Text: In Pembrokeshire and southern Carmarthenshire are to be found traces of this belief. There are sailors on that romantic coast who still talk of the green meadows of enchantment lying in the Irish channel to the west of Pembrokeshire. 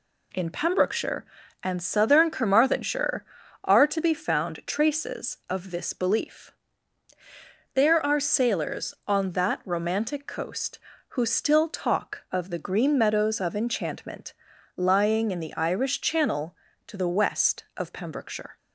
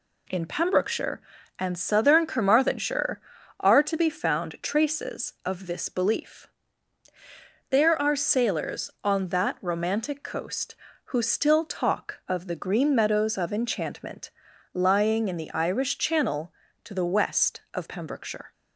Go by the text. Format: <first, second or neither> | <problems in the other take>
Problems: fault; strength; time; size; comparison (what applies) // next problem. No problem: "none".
neither | pauses between "enchantment" and "lying"; the same in both